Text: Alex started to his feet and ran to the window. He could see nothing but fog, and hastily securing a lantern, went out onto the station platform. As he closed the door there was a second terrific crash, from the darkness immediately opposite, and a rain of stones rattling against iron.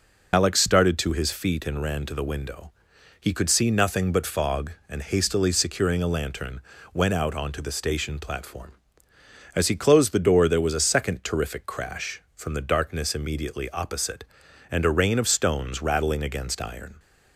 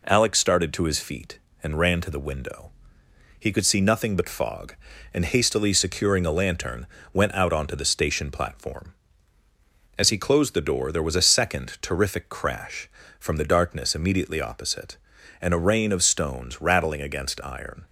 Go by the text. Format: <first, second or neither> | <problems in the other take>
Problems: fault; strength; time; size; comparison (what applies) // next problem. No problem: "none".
second | loses the start of "Alex"; at 0.3 s; 60 ms